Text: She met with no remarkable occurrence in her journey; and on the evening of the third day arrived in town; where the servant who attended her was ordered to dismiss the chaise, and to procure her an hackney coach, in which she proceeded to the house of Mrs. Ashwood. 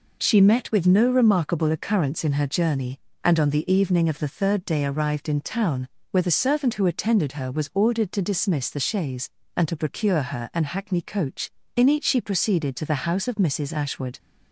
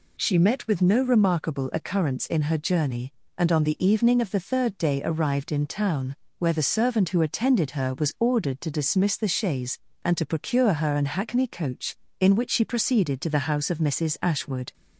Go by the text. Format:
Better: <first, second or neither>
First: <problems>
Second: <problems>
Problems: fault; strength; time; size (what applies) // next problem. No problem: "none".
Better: second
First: says "each" for "which"; at 11.8 s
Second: none